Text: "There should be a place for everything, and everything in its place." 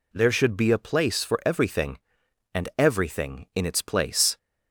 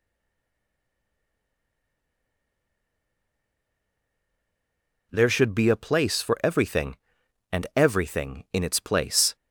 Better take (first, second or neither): first